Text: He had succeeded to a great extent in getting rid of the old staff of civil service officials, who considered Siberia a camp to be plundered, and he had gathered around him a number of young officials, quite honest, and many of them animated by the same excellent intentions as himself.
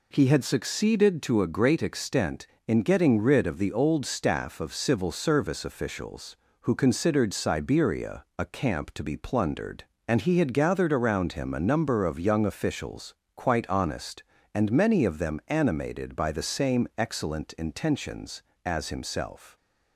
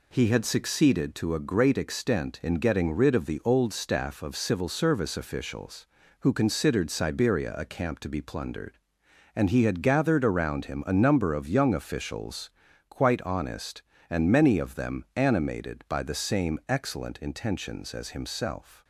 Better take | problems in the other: neither | none

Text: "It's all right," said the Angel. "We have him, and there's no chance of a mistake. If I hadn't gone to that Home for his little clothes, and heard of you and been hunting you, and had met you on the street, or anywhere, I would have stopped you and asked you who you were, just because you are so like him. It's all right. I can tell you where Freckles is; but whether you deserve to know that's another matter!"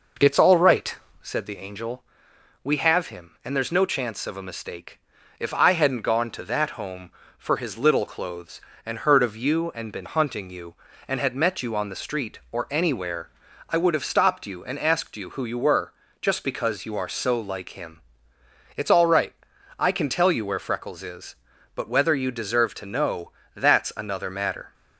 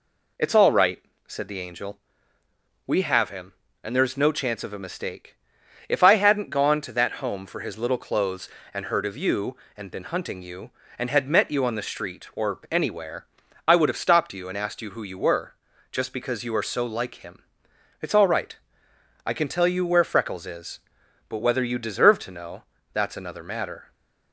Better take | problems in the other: second | starts louder than the rest; noticeable; until 1.3 s; 5.5 dB // pauses between "know" and "that's"; slight; at 23.3 s; 0.22 s long; slight in the second

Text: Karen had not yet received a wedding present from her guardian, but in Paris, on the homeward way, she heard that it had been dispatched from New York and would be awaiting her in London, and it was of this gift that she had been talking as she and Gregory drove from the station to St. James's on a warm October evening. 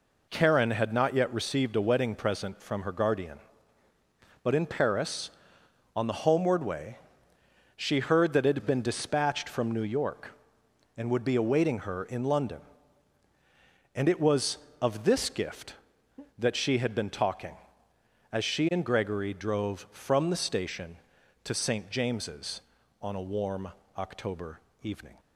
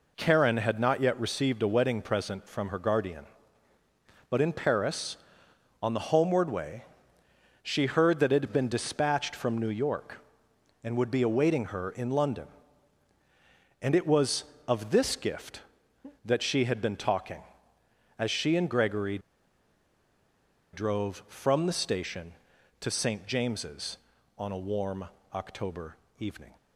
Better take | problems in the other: first | pauses between "Gregory" and "drove"; strong; at 19.1 s; 1.5 s long // pauses between "warm" and "October"; slight; at 25.0 s; 0.28 s long; slight in the first // pauses between "October" and "evening"; slight; at 25.9 s; 0.24 s long; slight in the first

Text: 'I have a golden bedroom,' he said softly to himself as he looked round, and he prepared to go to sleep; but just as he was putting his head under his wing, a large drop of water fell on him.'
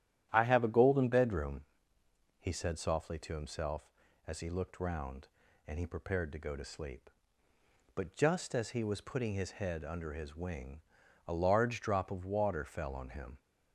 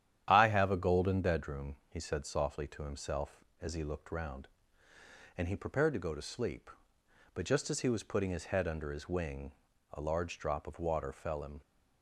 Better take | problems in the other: first | starts louder than the rest; strong; until 1.3 s; 10 dB; strong in the first // skips "on"; at 11.4 s

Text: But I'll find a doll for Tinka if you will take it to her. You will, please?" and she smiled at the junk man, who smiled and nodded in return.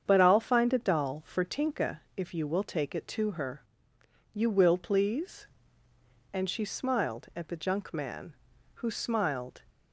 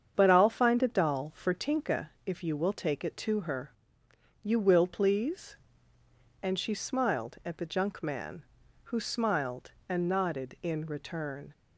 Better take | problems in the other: second | starts louder than the rest; strong; until 1.0 s; 7.5 dB; strong in the second // stops before "and nodded in return"; at 9.7 s

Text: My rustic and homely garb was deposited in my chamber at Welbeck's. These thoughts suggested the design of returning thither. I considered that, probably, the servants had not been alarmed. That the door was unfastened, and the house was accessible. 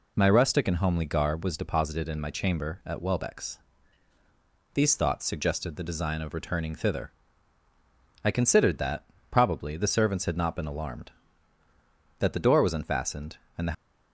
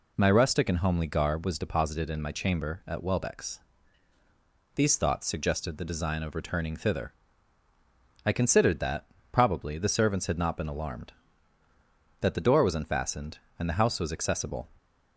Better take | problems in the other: second | stops before "house was accessible"; at 13.7 s

